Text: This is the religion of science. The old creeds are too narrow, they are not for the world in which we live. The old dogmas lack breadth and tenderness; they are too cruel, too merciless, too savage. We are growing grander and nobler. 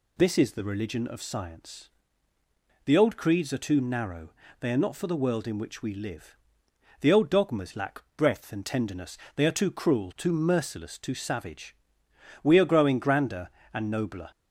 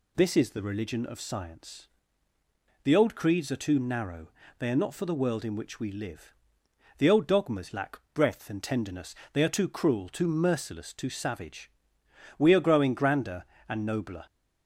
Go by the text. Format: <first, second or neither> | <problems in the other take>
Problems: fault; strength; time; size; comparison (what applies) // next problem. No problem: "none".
neither | pauses between "lack" and "breadth"; slight; the same in both